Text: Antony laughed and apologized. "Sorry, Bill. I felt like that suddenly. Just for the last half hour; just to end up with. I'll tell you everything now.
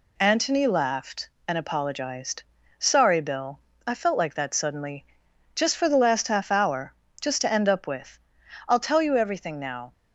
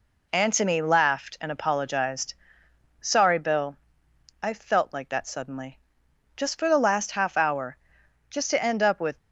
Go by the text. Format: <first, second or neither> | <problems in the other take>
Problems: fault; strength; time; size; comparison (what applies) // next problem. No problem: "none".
first | stops before "I'll tell you everything now"; at 9.1 s